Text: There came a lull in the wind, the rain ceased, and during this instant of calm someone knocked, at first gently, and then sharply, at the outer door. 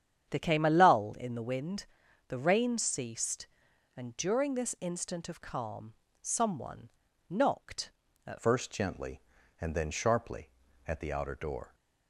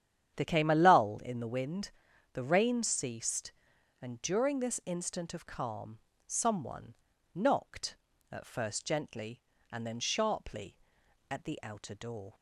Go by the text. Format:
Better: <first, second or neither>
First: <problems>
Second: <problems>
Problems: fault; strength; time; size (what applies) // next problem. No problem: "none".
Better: second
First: starts louder than the rest; strong; until 1.3 s; 8.5 dB // pauses between "calm" and "someone"; slight; at 5.9 s; 0.28 s long // pauses between "someone" and "knocked"; at 6.8 s; 0.40 s long // changes voice at "first"; from 8.4 s on; 3.3 s long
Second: starts louder than the rest; strong; until 1.4 s; 9.5 dB // pauses between "calm" and "someone"; slight; at 5.9 s; 0.28 s long // pauses between "someone" and "knocked"; at 6.9 s; 0.40 s long